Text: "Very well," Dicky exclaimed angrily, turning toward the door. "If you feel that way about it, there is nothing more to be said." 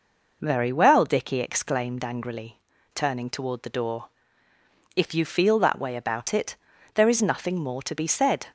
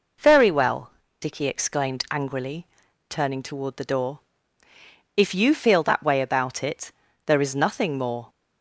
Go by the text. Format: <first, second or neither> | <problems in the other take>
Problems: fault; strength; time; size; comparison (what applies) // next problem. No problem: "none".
first | stops before "to be said"; at 8.2 s